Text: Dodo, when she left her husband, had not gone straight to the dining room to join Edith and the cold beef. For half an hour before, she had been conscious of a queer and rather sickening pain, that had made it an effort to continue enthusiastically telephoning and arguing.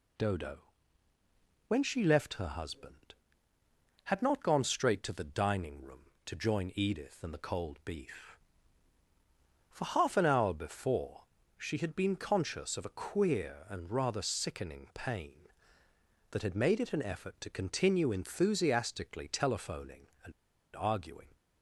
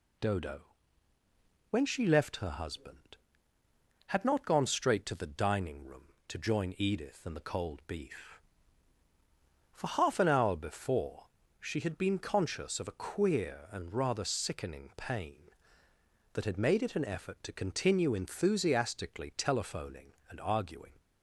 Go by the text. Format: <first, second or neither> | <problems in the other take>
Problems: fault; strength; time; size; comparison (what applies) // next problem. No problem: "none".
second | pauses between "and" and "arguing"; at 20.3 s; 0.44 s long